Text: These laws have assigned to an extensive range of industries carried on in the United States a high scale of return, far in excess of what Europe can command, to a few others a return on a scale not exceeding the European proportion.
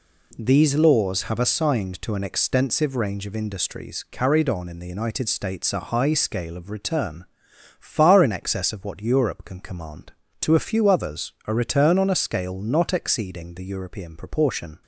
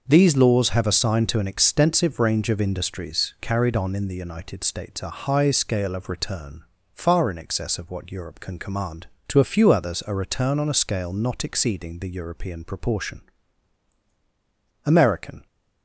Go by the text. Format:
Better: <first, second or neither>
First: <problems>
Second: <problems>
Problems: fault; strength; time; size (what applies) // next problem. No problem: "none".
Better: first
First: none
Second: starts louder than the rest; noticeable; until 1.0 s; 6 dB // goes on to say "American"; noticeable; from 14.8 s on; 0.62 s long